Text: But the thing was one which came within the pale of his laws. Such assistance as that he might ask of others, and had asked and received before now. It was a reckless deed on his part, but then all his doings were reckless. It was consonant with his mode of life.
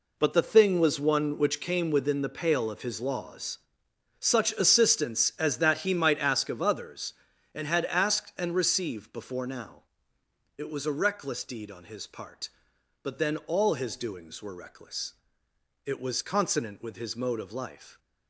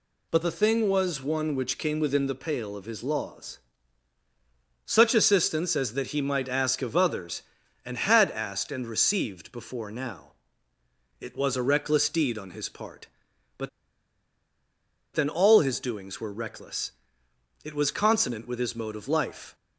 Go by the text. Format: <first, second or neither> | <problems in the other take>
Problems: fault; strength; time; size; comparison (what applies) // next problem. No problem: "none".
first | pauses between "but" and "then"; strong; at 13.6 s; 1.4 s long